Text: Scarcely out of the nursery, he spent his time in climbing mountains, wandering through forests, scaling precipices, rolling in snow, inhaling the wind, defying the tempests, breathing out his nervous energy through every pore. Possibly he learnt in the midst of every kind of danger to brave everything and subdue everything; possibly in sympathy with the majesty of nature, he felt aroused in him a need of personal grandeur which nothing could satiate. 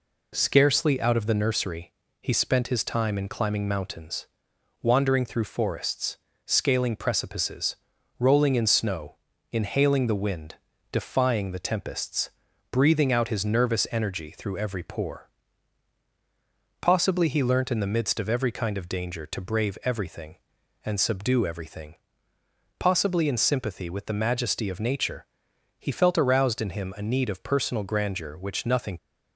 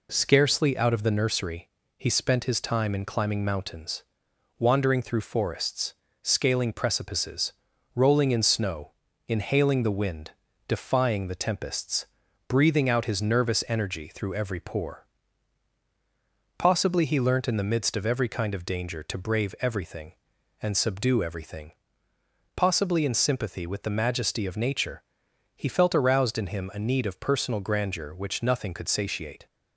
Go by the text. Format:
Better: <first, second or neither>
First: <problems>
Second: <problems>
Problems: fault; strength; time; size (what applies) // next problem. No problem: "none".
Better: second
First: stops before "could satiate"; at 28.9 s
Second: none